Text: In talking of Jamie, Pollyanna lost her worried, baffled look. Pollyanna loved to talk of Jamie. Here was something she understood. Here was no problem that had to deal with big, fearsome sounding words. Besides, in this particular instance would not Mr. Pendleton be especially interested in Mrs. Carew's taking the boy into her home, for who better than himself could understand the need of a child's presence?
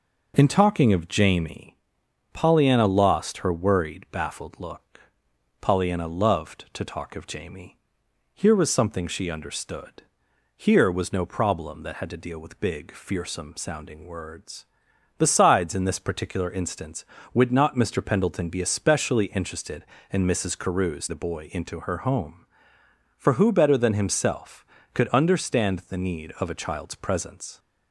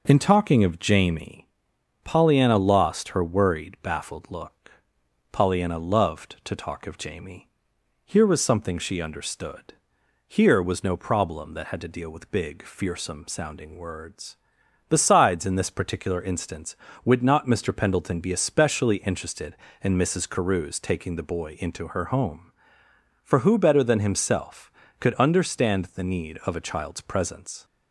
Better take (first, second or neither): second